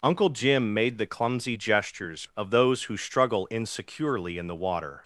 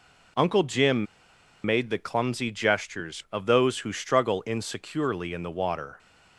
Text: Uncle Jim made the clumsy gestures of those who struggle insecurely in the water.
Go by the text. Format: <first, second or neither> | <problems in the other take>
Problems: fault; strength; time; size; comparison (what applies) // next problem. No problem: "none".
first | pauses between "Jim" and "made"; noticeable; at 1.0 s; 0.60 s long